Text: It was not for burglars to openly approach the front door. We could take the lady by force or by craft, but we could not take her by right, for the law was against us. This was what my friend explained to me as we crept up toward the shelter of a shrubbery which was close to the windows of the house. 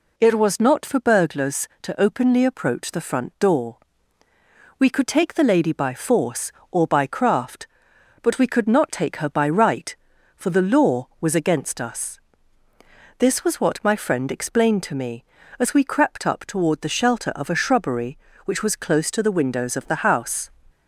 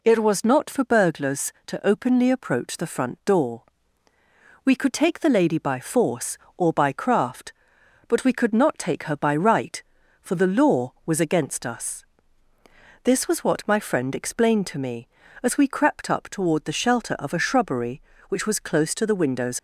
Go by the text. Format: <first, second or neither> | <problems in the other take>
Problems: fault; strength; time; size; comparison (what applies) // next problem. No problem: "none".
first | stops before "of the house"; at 19.5 s